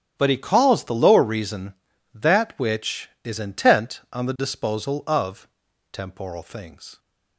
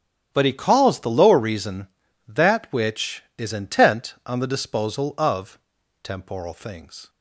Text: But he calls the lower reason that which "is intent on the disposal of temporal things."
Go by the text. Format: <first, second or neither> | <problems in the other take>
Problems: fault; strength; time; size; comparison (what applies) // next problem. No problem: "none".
neither | starts louder than the rest; strong; the same in both // pauses between "of" and "temporal"; noticeable; the same in both